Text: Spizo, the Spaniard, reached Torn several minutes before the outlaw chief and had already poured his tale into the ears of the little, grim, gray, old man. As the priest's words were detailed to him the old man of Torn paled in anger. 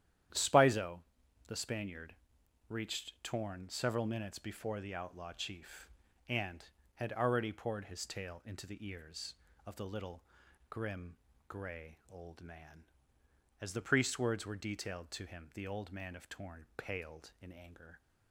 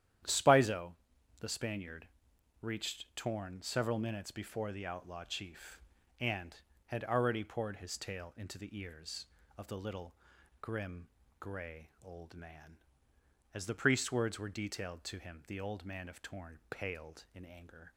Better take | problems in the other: neither | starts louder than the rest; strong; the same in both

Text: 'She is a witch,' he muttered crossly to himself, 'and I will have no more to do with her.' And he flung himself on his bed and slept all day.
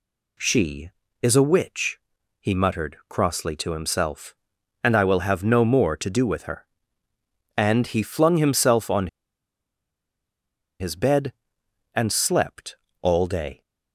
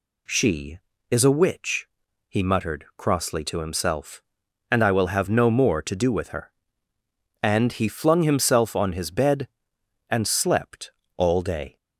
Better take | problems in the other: second | pauses between "on" and "his"; strong; at 9.0 s; 1.7 s long // pauses between "slept" and "all"; slight; at 12.7 s; 0.26 s long; slight in the second

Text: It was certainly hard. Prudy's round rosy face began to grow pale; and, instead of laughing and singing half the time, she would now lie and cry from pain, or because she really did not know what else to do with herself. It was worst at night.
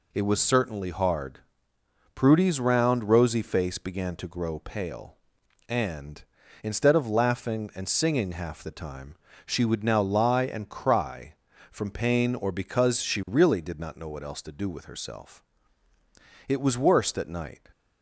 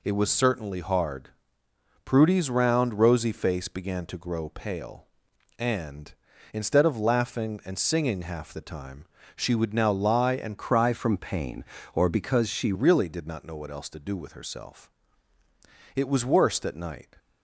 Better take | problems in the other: first | changes voice from "cry" to "she"; from 10.5 to 12.7 s; 2.2 s long

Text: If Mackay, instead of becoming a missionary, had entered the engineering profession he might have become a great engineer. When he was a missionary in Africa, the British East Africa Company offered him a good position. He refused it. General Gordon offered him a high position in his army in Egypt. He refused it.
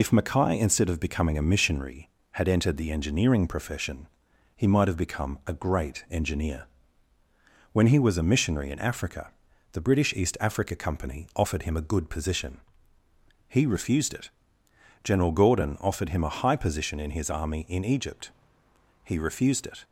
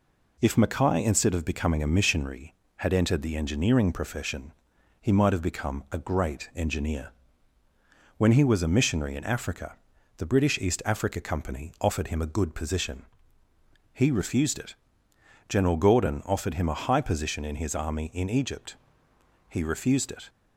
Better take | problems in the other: second | loses the start of "If"; at 0.0 s; 55 ms // pauses between "profession" and "he"; noticeable; at 4.0 s; 0.48 s long; noticeable in the second

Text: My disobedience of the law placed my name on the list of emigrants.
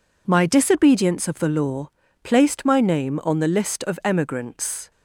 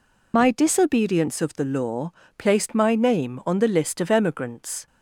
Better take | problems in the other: first | loses the start of "My"; at 0.3 s; 60 ms // pauses between "law" and "placed"; slight; at 2.1 s; 0.28 s long; slight in the first

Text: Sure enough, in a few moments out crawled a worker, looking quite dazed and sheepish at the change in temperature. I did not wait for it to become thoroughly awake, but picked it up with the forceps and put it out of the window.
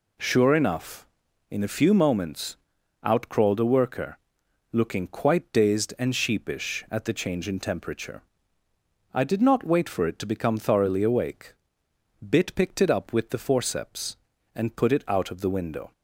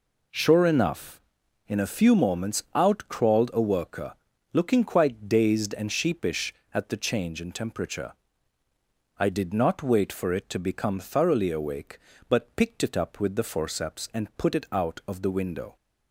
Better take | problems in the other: second | pauses between "moments" and "out"; noticeable; at 2.5 s; 0.48 s long // says "bit" for "but"; at 12.1 s

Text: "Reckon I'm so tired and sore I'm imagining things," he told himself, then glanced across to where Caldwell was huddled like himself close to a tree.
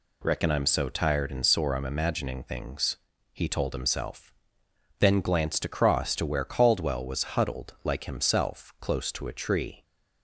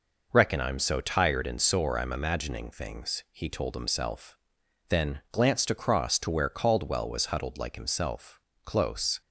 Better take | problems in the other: first | pauses between "himself" and "close"; slight; at 8.3 s; 0.24 s long // stops before "to a tree"; at 9.2 s

